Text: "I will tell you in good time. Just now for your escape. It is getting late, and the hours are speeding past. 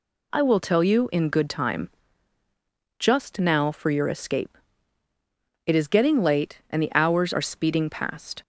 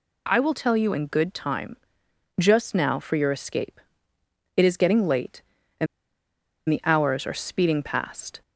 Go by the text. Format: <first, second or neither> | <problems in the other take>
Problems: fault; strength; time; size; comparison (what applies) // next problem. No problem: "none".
first | pauses between "and" and "the"; noticeable; at 5.8 s; 0.83 s long